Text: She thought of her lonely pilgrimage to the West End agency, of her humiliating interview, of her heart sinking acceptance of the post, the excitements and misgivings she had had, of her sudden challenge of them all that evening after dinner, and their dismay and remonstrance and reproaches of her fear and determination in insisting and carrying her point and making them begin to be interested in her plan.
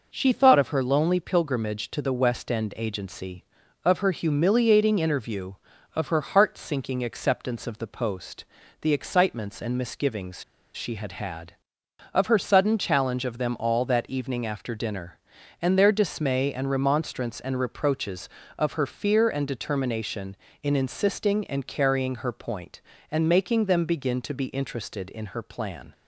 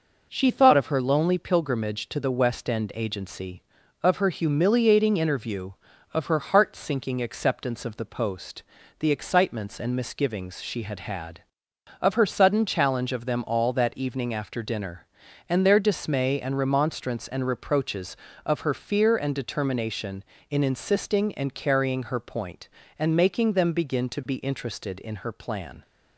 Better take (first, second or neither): second